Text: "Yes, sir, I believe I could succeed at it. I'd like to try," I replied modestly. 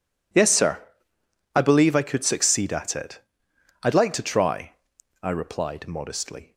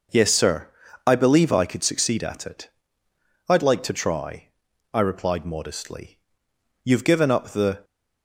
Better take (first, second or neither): first